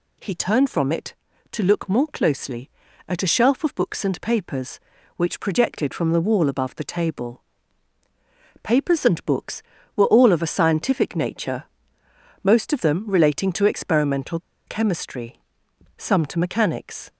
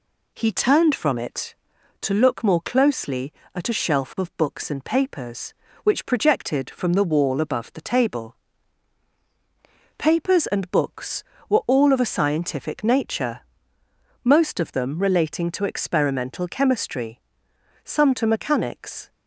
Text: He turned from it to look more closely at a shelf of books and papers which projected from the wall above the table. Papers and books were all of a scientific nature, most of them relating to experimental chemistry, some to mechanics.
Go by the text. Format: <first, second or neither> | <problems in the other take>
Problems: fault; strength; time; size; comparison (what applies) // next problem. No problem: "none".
second | pauses between "experimental" and "chemistry"; slight; at 14.3 s; 0.27 s long